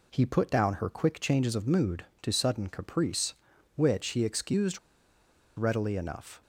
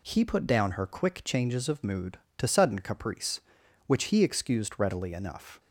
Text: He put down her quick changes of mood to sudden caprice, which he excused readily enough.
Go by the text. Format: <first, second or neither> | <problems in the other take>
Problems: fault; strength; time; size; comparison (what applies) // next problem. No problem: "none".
second | pauses between "excused" and "readily"; noticeable; at 4.7 s; 0.78 s long